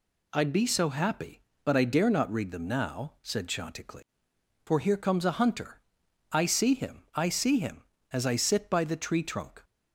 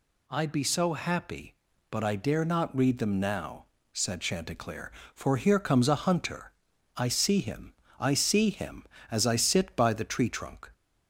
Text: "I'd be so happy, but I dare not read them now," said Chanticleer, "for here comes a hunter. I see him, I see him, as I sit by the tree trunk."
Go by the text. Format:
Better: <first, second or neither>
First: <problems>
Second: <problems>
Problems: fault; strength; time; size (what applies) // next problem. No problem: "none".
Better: neither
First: none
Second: none